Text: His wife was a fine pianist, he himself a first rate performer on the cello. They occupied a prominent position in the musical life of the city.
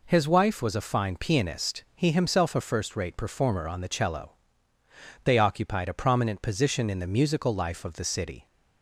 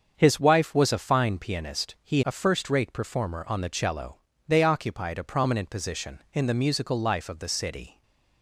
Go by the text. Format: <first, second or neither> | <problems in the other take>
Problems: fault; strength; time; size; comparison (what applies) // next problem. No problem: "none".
first | starts louder than the rest; until 1.1 s; 7 dB // skips "himself"; at 2.2 s // stays silent after the last word; slight; from 7.9 s on; 0.5 s long